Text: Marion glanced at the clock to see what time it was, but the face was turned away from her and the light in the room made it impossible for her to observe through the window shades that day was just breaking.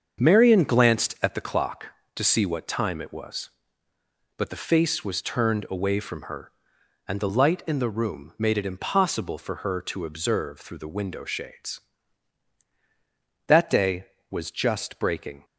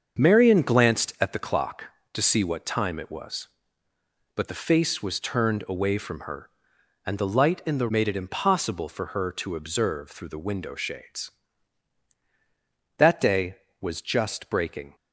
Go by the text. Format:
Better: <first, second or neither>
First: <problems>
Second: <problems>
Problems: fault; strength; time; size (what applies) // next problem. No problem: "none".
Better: first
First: starts louder than the rest; until 1.2 s; 7 dB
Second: starts louder than the rest; until 1.2 s; 6.5 dB // skips "room"; at 7.8 s